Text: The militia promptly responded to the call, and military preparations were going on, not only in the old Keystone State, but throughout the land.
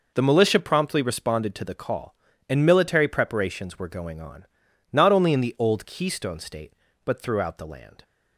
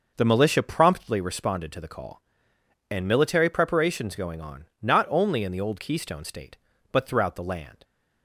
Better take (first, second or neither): first